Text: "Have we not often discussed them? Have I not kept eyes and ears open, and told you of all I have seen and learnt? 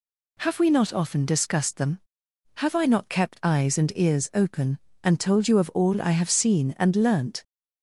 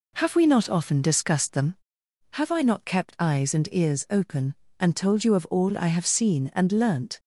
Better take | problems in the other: first | starts louder than the rest; until 2.0 s; 3.5 dB

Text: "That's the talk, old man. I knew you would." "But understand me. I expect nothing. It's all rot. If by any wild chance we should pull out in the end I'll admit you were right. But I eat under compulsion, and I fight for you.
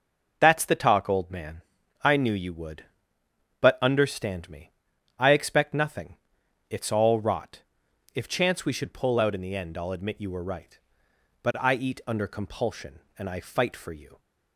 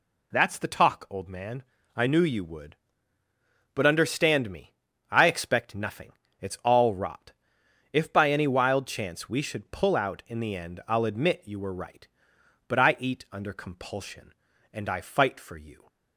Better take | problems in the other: second | skips "by any wild"; at 8.2 s

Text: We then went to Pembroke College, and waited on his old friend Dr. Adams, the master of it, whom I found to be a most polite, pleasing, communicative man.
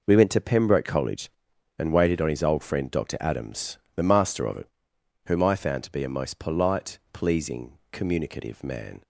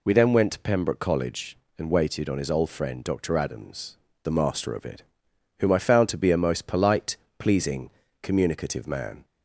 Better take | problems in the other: second | skips "then"; at 0.1 s

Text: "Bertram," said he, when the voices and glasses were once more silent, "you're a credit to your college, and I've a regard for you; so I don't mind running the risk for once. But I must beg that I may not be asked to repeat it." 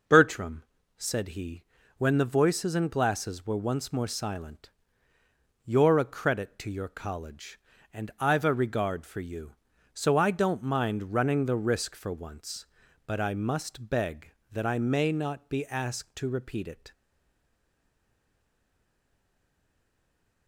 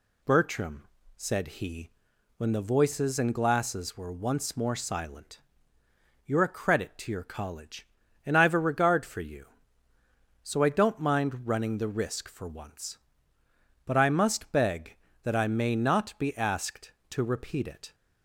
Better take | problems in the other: second | stays silent after the last word; strong; from 16.9 s on; 3.5 s long

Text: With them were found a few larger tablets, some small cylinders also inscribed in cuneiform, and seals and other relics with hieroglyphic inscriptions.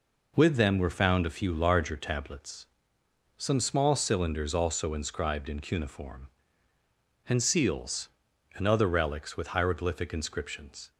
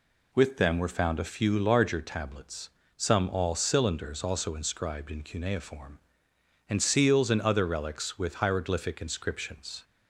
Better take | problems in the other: first | says "all" for "small"; at 3.2 s

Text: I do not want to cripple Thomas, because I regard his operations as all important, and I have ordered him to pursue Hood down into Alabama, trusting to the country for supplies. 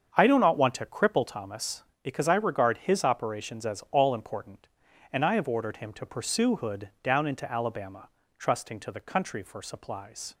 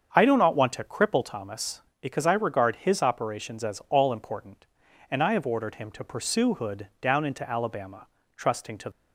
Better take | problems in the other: first | starts louder than the rest; strong; until 1.1 s; 7 dB; strong in the first // stops before "the country for supplies"; at 8.9 s

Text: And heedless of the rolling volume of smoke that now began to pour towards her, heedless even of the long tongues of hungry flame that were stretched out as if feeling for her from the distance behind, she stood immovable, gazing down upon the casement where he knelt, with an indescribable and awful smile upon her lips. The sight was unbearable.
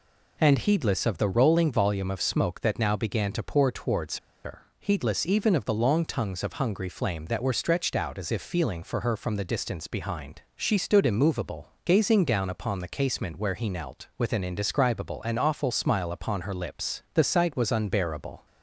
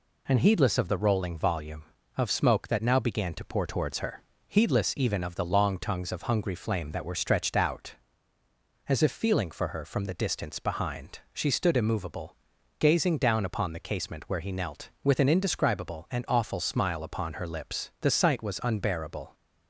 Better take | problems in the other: second | pauses between "towards" and "her"; slight; at 4.1 s; 0.26 s long

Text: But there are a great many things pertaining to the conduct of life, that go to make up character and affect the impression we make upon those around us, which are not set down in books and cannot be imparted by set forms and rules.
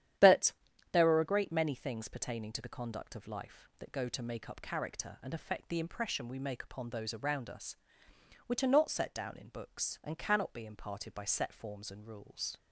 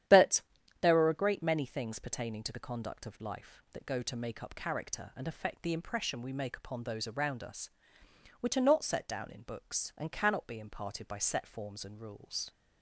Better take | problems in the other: neither | starts louder than the rest; strong; the same in both // pauses between "But" and "there"; the same in both

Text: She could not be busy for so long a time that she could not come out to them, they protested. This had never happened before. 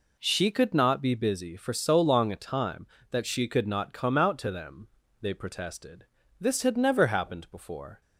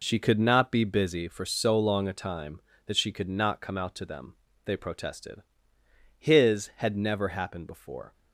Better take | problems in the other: first | says "His" for "This"; at 6.1 s

